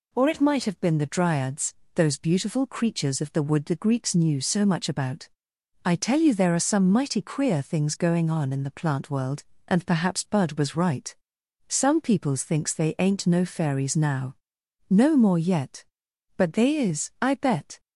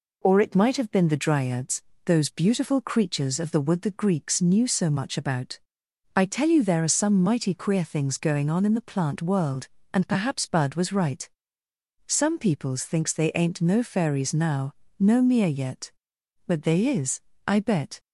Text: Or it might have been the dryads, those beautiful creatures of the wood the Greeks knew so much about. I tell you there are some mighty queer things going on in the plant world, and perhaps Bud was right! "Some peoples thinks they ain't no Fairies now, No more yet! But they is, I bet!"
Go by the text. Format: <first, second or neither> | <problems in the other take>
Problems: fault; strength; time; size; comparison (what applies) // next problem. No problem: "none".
first | says "mere" for "more"; at 15.2 s